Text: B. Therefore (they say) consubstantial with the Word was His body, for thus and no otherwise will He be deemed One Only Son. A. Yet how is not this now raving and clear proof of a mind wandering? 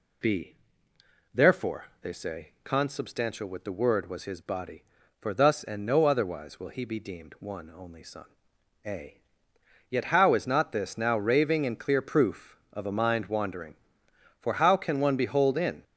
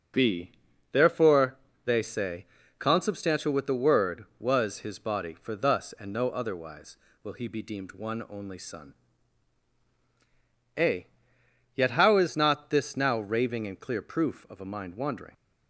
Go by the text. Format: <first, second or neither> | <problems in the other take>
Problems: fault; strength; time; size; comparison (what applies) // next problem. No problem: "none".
second | goes on to say "for how can one behold in"; from 14.3 s on; 1.4 s long